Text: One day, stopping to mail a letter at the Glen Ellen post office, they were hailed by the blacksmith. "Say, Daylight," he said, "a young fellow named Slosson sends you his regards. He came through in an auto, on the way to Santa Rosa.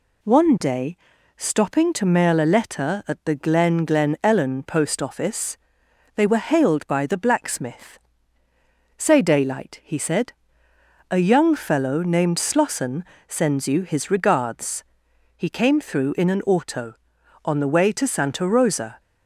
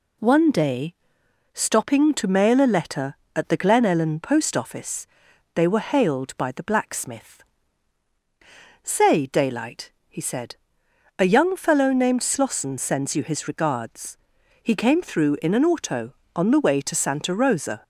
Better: second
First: says "Glen" twice; at 3.8 s // pauses between "Slosson" and "sends"; slight; at 13.0 s; 0.24 s long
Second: none

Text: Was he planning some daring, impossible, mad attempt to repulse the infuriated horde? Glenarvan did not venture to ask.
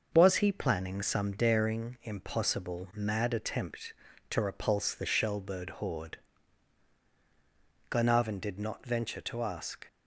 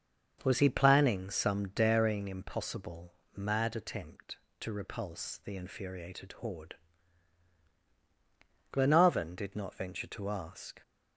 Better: second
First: starts louder than the rest; noticeable; until 1.1 s; 6 dB // says "shellbird" for "infuriated"; at 5.0 s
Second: starts louder than the rest; until 1.4 s; 6.5 dB

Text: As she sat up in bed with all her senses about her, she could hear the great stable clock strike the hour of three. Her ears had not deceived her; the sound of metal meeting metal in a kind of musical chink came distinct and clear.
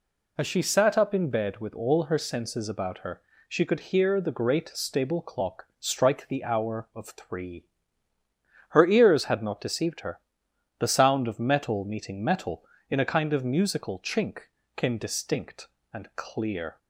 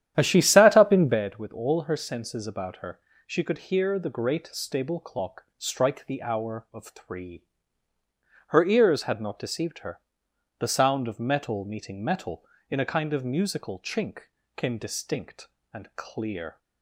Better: first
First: pauses between "chink" and "came"; slight; at 14.4 s; 0.34 s long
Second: starts louder than the rest; strong; until 1.2 s; 10.5 dB // pauses between "chink" and "came"; slight; at 14.2 s; 0.34 s long

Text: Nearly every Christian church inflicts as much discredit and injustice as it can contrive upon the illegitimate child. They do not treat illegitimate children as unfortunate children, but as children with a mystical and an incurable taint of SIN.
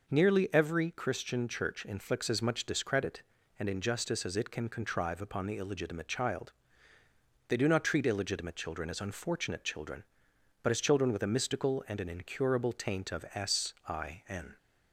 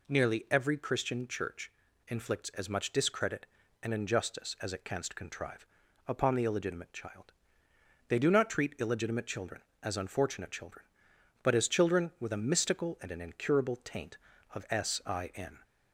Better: first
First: none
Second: pauses between "church" and "inflicts"; slight; at 1.7 s; 0.35 s long // says "canst" for "can"; at 4.8 s // pauses between "contrive" and "upon"; at 5.6 s; 0.40 s long

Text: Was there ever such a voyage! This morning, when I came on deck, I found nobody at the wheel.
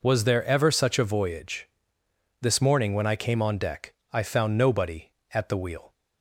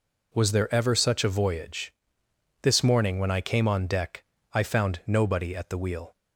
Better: neither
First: none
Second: none

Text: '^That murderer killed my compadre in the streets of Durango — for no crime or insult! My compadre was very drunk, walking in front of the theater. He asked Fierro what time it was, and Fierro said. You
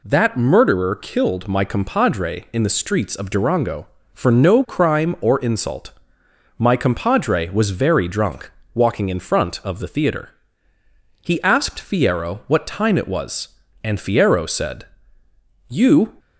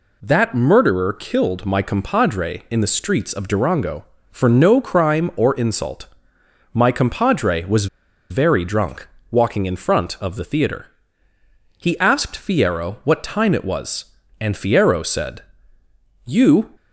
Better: first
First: none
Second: pauses between "was" and "very"; at 7.8 s; 0.44 s long

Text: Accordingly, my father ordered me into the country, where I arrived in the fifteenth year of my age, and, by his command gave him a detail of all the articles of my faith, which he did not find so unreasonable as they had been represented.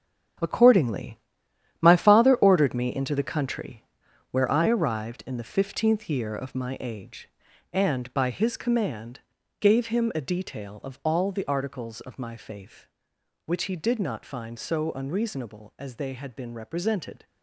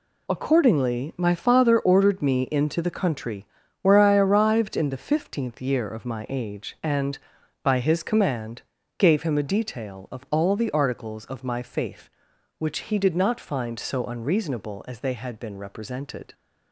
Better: second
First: gets quieter; strong; throughout; 10.5 dB // pauses between "command" and "gave"; at 9.1 s; 0.40 s long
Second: pauses between "command" and "gave"; slight; at 8.6 s; 0.36 s long

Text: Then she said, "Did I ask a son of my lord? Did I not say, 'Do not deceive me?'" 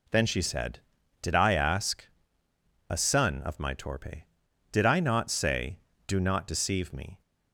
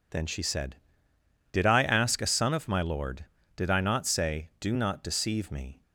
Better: second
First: pauses between "ask" and "a"; noticeable; at 2.0 s; 0.84 s long // says "torpe" for "lord"; at 3.7 s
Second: none

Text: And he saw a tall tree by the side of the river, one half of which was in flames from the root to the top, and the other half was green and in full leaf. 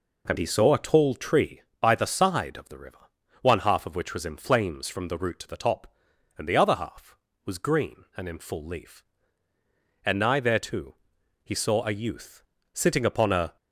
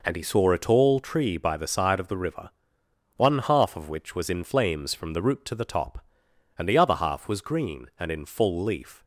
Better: second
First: goes on to say "And nigh thereto he saw a youth sitting upon a"; strong; from 10.0 s on; 3.5 s long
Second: none

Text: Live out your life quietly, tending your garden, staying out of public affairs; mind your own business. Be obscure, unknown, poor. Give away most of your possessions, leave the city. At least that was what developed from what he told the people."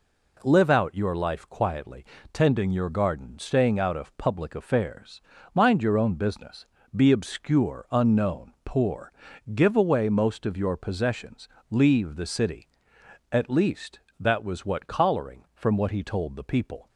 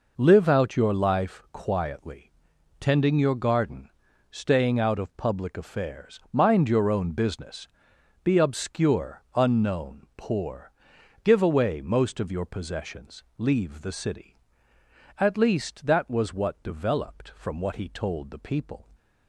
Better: second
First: says "collaring" for "developed"; at 14.8 s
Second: none

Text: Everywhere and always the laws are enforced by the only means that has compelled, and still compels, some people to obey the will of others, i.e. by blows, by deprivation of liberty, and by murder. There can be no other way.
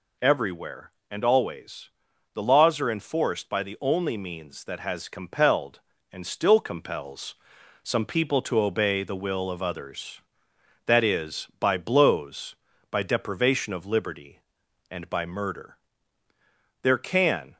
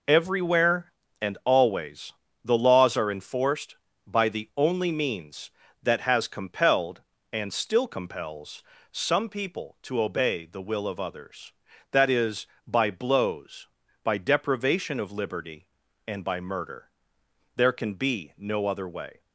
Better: second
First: pauses between "always" and "the"; at 1.8 s; 0.44 s long // stops before "be no other way"; at 17.5 s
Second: pauses between "always" and "the"; slight; at 2.1 s; 0.32 s long

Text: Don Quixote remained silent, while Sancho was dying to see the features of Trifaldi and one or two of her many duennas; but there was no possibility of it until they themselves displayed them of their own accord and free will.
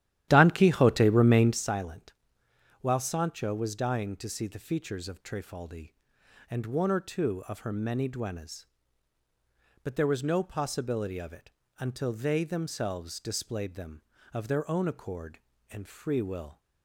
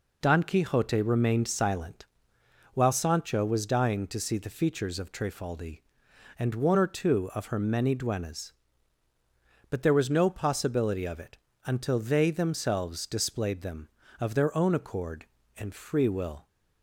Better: second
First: starts louder than the rest; strong; until 1.7 s; 12.5 dB // pauses between "it" and "until"; slight; at 11.5 s; 0.26 s long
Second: pauses between "it" and "until"; slight; at 11.3 s; 0.26 s long

